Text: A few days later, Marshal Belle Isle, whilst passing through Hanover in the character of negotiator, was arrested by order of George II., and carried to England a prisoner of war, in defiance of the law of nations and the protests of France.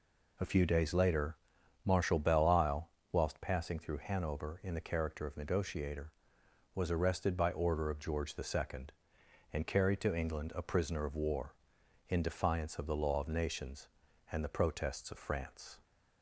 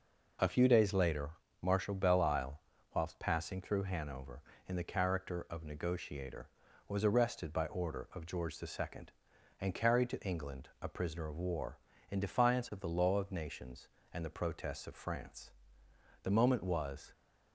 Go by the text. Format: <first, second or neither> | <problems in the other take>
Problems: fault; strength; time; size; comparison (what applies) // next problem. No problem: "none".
first | goes on to say "The moment was"; noticeable; from 16.2 s on; 0.88 s long